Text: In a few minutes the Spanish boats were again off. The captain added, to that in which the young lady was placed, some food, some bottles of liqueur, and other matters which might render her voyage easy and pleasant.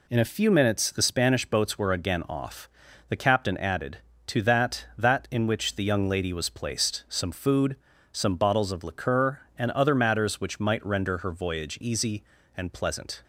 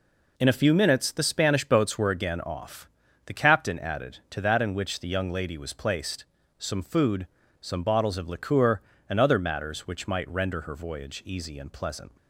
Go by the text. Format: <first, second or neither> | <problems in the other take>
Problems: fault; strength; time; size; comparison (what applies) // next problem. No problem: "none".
second | says "that" twice; at 4.9 s